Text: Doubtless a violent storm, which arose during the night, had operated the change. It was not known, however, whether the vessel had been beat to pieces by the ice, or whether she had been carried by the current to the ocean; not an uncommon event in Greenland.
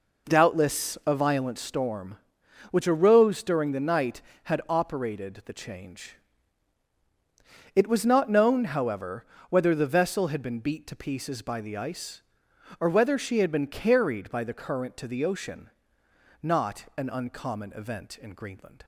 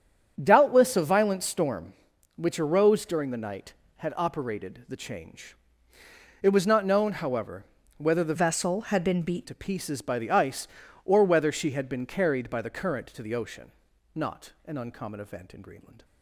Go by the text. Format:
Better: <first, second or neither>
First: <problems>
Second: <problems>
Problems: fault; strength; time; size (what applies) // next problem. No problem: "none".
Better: first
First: none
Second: starts louder than the rest; strong; until 1.4 s; 7.5 dB // changes voice from "vessel" to "beat"; from 8.3 to 9.4 s; 1.1 s long